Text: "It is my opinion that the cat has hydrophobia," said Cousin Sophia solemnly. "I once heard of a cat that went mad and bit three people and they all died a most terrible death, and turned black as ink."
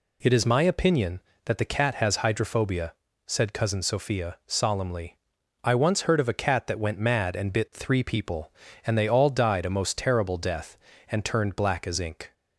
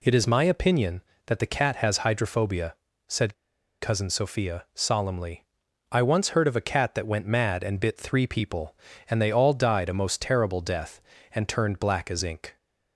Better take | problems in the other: first | pauses between "said" and "Cousin"; noticeable; at 3.3 s; 0.46 s long

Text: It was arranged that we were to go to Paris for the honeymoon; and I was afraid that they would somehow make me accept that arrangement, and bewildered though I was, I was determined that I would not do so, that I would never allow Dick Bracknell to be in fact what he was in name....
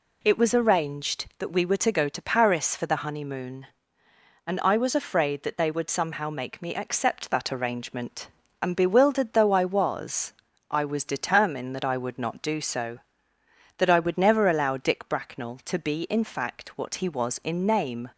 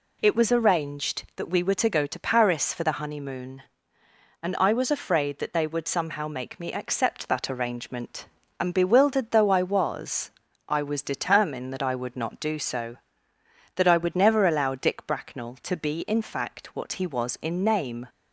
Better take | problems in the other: neither | none

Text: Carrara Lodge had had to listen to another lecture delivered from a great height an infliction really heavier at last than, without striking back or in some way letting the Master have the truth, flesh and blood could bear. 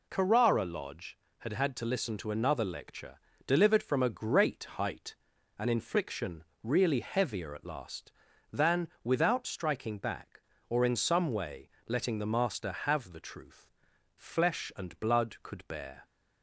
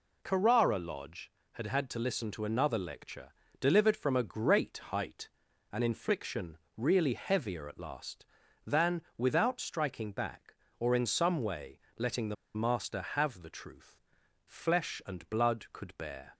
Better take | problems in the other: first | pauses between "lecture" and "delivered"; slight; at 3.3 s; 0.28 s long; slight in the first // pauses between "height" and "an"; at 5.2 s; 0.44 s long; also in the first // pauses between "infliction" and "really"; slight; at 6.5 s; 0.20 s long; slight in the first // pauses between "way" and "letting"; slight; at 11.7 s; 0.20 s long; slight in the first // pauses between "the" and "Master"; slight; at 12.3 s; 0.21 s long

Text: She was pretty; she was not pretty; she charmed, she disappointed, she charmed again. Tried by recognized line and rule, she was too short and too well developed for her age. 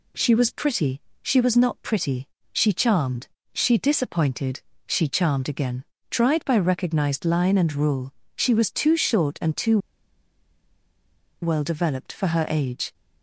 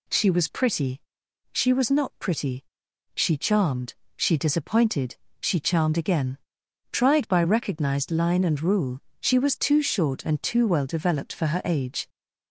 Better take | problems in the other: second | pauses between "too" and "well"; strong; at 9.7 s; 1.6 s long

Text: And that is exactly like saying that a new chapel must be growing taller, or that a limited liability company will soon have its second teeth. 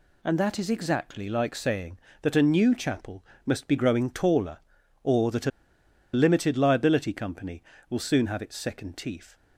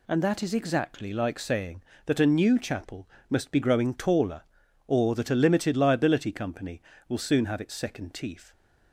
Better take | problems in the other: second | pauses between "chapel" and "must"; slight; at 3.2 s; 0.22 s long; slight in the second // pauses between "a" and "limited"; noticeable; at 5.5 s; 0.64 s long

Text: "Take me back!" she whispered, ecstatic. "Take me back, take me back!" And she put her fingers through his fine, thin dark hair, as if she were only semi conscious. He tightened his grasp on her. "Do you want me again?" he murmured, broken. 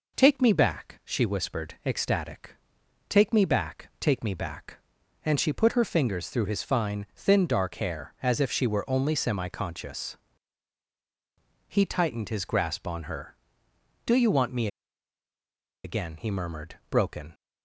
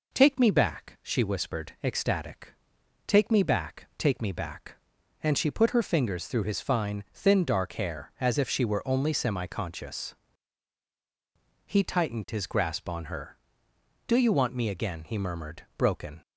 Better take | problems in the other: second | pauses between "me" and "again"; at 14.6 s; 1.1 s long

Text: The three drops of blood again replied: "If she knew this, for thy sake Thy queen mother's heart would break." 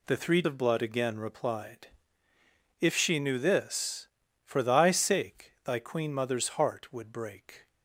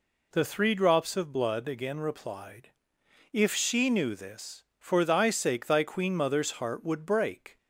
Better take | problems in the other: second | skips "drops"; at 0.4 s

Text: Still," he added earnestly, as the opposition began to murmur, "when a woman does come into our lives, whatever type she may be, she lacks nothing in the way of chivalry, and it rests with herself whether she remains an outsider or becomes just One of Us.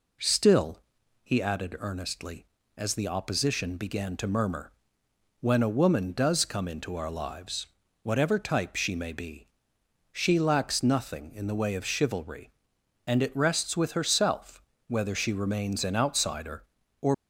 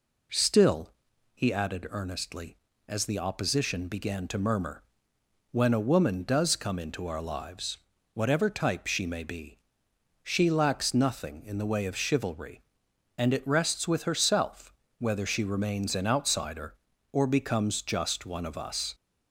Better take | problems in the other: second | pauses between "herself" and "whether"; slight; at 14.6 s; 0.26 s long; slight in the second // stops before "becomes just One of Us"; at 17.1 s

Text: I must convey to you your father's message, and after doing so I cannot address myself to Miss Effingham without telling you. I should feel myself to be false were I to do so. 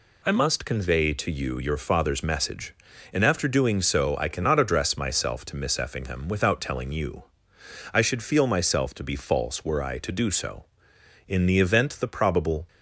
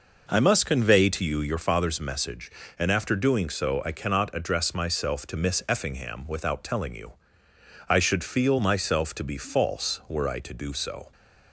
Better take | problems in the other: second | goes on to say "In the event the probable"; from 11.2 s on; 1.4 s long

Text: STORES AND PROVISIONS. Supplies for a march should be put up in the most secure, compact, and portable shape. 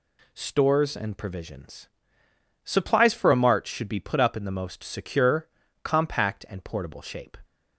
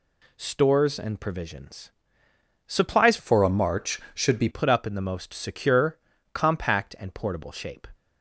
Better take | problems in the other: first | changes voice from "for" to "be"; from 3.1 to 4.4 s; 1.3 s long

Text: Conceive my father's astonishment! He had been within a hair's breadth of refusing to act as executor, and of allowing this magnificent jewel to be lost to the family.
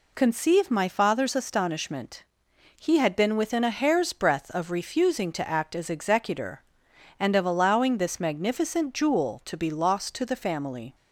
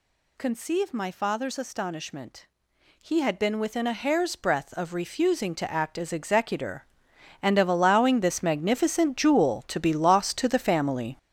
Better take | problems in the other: first | gets louder; strong; throughout; 8.5 dB

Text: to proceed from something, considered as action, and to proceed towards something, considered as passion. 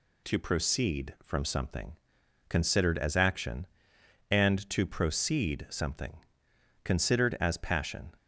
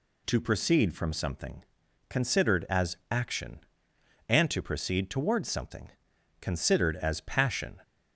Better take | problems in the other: second | skips "towards"; at 5.6 s

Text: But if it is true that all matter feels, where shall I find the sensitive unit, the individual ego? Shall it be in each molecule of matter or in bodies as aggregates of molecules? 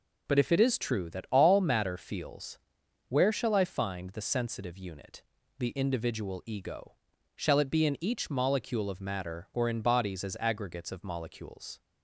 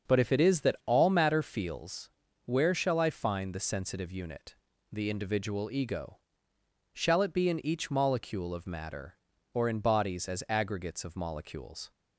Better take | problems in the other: first | starts louder than the rest; until 1.1 s; 6.5 dB // skips "true"; at 0.6 s

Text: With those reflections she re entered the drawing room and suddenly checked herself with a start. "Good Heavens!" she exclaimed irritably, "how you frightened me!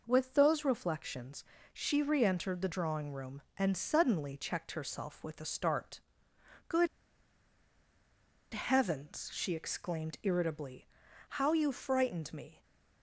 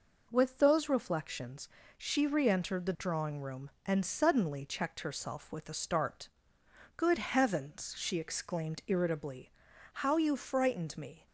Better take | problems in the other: second | pauses between "reflections" and "she"; slight; at 1.4 s; 0.28 s long; slight in the second // pauses between "Good" and "Heavens"; strong; at 6.8 s; 1.6 s long

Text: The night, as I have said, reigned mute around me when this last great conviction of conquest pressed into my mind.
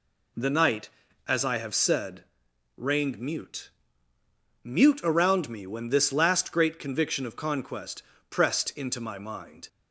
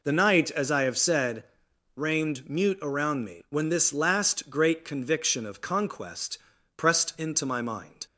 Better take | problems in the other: second | says "mute" twice; at 4.6 s // pauses between "conquest" and "pressed"; slight; at 8.0 s; 0.30 s long; also in the second

